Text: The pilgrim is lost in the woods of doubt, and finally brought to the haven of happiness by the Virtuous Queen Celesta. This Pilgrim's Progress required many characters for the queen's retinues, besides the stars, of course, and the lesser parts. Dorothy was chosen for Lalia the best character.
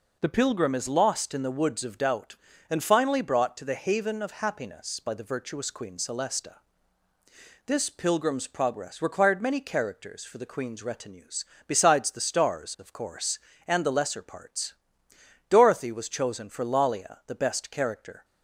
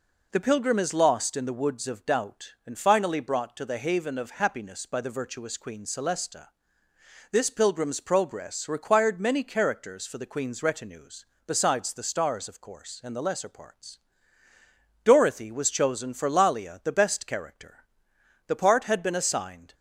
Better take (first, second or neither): first